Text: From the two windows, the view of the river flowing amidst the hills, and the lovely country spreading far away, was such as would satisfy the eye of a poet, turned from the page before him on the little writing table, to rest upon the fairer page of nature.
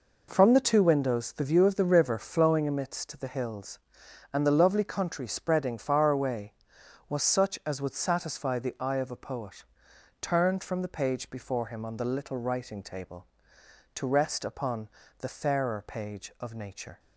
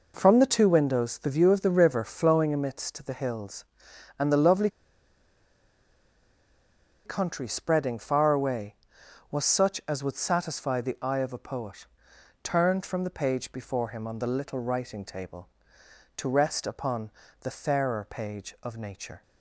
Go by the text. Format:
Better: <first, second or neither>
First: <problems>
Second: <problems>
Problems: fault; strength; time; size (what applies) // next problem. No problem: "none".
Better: first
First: pauses between "upon" and "the"; slight; at 14.8 s; 0.30 s long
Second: pauses between "lovely" and "country"; strong; at 4.6 s; 2.3 s long // pauses between "upon" and "the"; slight; at 17.1 s; 0.30 s long